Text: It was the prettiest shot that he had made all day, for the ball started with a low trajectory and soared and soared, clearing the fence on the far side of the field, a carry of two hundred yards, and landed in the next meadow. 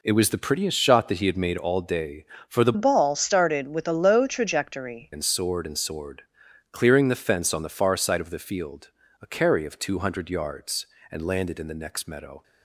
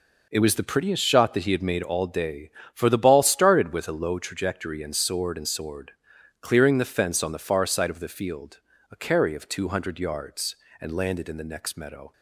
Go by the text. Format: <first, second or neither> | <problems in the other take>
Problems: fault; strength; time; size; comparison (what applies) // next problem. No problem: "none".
second | changes voice from "ball" to "trajectory"; from 2.7 to 5.1 s; 2.4 s long